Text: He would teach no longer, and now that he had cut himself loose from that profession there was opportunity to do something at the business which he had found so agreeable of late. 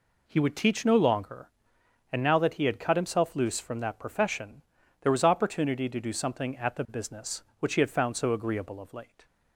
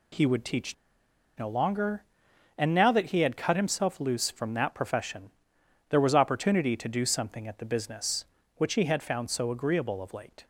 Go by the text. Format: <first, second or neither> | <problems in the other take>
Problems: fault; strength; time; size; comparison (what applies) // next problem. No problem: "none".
first | pauses between "teach" and "no"; noticeable; at 0.7 s; 0.64 s long // pauses between "profession" and "there"; noticeable; at 5.2 s; 0.60 s long; also in the first